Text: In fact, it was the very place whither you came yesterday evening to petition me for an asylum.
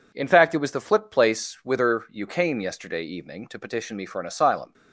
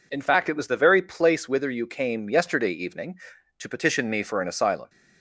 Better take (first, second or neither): second